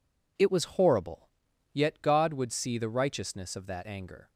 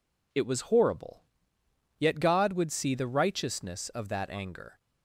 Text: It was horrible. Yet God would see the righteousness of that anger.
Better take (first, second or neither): neither